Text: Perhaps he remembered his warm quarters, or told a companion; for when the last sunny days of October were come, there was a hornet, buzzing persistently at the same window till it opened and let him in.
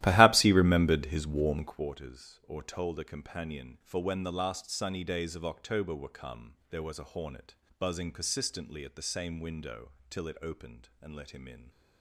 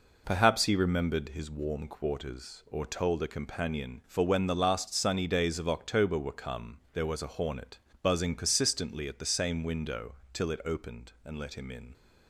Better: second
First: starts louder than the rest; strong; until 1.9 s; 14.5 dB // pauses between "window" and "till"; slight; at 9.9 s; 0.18 s long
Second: pauses between "window" and "till"; slight; at 10.1 s; 0.18 s long

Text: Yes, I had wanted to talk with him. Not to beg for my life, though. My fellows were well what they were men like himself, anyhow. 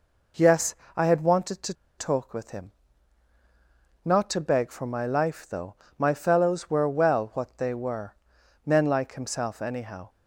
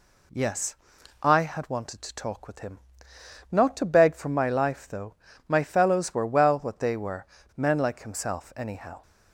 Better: second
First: pauses between "to" and "talk"; slight; at 1.7 s; 0.24 s long // pauses between "were" and "men"; noticeable; at 8.1 s; 0.50 s long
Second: pauses between "were" and "men"; slight; at 7.2 s; 0.31 s long

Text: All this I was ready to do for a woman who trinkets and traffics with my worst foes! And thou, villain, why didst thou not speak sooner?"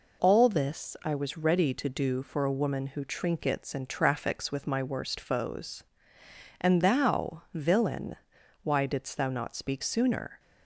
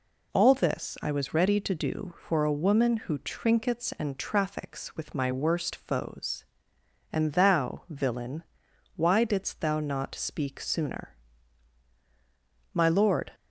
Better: first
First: none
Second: goes on to say "My lord"; from 12.7 s on; 0.58 s long

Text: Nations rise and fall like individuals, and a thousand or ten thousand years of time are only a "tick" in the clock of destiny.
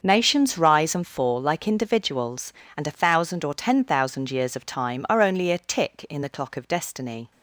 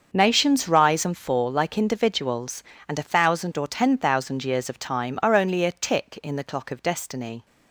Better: neither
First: starts louder than the rest; until 1.0 s; 6.5 dB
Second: starts louder than the rest; until 1.1 s; 6.5 dB

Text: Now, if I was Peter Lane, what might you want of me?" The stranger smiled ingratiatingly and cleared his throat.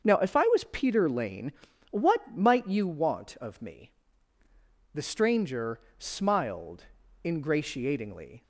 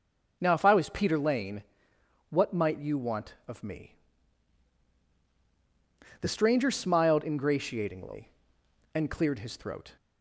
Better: second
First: starts louder than the rest; until 1.0 s; 7 dB // pauses between "stranger" and "smiled"; slight; at 5.7 s; 0.18 s long // pauses between "smiled" and "ingratiatingly"; at 6.8 s; 0.38 s long // stops before "and cleared his throat"; at 8.4 s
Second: none

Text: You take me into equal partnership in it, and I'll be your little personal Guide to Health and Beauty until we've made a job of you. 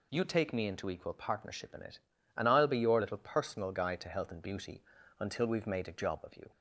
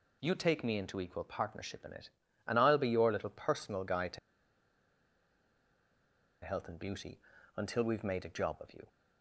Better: first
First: pauses between "Beauty" and "until"; at 4.8 s; 0.38 s long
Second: pauses between "to" and "Health"; strong; at 4.1 s; 2.2 s long // pauses between "Beauty" and "until"; at 7.1 s; 0.38 s long

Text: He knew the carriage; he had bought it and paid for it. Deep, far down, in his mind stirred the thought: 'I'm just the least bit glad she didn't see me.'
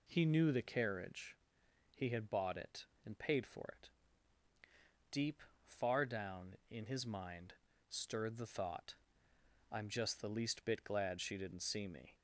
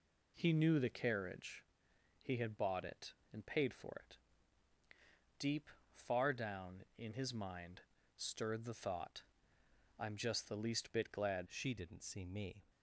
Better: first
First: pauses between "mind" and "stirred"; slight; at 7.5 s; 0.34 s long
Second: pauses between "mind" and "stirred"; slight; at 7.8 s; 0.34 s long // changes voice at "she"; from 11.4 s on; 1.2 s long

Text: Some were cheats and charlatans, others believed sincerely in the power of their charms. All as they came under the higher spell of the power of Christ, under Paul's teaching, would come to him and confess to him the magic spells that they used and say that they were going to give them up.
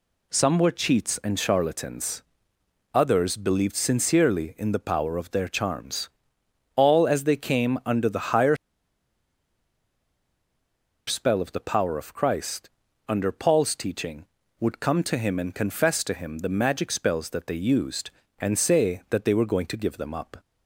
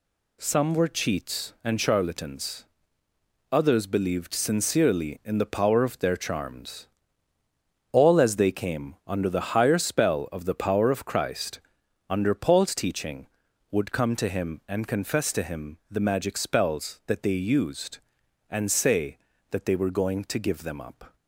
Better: second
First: pauses between "higher" and "spell"; strong; at 8.5 s; 2.5 s long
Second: none

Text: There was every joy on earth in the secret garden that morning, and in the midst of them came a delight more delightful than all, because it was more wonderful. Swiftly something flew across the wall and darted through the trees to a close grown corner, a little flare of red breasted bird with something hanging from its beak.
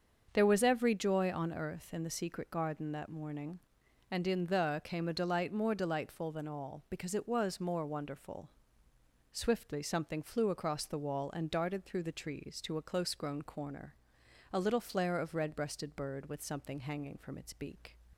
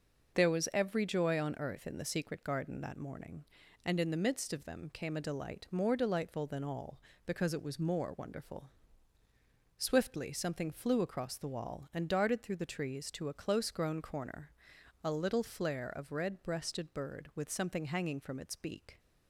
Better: second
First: starts louder than the rest; until 1.3 s; 6.5 dB // skips "midst of them"; at 4.8 s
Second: none

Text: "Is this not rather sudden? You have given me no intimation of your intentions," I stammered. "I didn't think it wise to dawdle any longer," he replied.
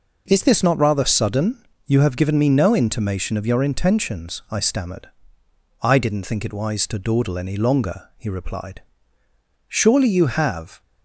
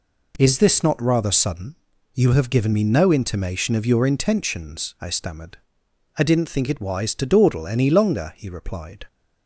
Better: second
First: goes on to say "Surely you have"; noticeable; from 9.6 s on; 1.1 s long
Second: none

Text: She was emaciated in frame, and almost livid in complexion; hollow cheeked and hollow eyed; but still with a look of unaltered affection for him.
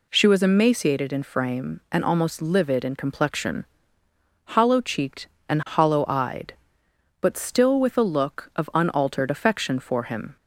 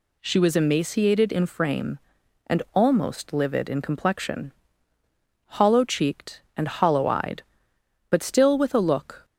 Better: first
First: none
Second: stops before "of unaltered affection for him"; at 9.2 s

